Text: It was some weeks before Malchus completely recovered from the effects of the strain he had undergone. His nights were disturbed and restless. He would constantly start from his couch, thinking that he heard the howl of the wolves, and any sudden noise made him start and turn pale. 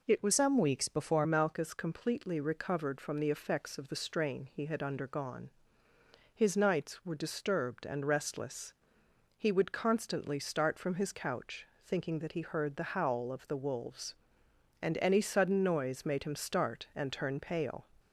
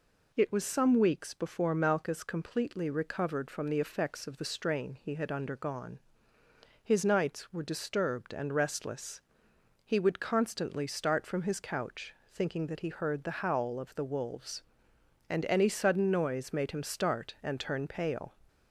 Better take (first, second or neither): second